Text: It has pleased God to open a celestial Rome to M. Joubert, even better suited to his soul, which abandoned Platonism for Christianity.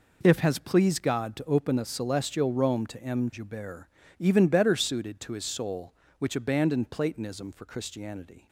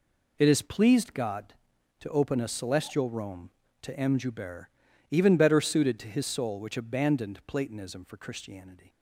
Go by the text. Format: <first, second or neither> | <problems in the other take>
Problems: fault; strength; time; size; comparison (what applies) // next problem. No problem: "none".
second | says "If" for "It"; at 0.2 s